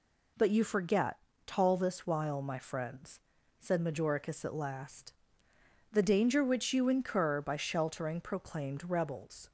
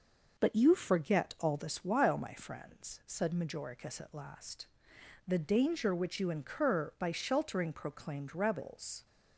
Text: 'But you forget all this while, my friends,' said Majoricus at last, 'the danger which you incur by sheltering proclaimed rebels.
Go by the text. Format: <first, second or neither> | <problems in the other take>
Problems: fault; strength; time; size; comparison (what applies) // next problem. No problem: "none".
second | says "tall" for "all"; at 1.4 s